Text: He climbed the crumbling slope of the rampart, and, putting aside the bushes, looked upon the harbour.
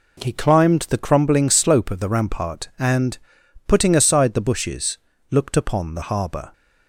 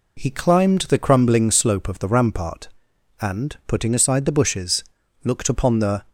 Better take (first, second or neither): first